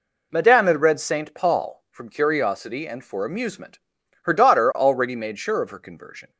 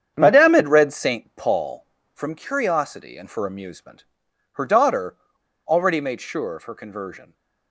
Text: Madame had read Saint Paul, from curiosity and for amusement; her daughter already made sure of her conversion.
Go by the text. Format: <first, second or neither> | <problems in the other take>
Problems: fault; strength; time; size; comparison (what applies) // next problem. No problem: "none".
first | starts louder than the rest; strong; until 1.1 s; 8.5 dB // pauses between "daughter" and "already"; noticeable; at 5.1 s; 0.51 s long